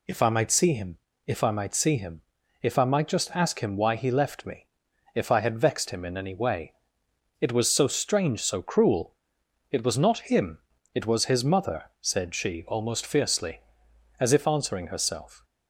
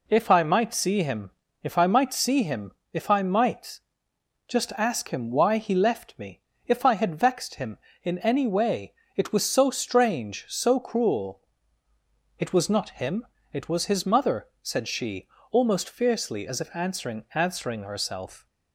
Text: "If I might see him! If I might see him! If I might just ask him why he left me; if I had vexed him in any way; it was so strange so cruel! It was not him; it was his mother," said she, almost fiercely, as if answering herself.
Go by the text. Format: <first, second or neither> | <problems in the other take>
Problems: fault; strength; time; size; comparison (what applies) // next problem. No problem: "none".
first | pauses between "might" and "just"; noticeable; at 3.7 s; 0.66 s long // says "answering" twice; at 17.3 s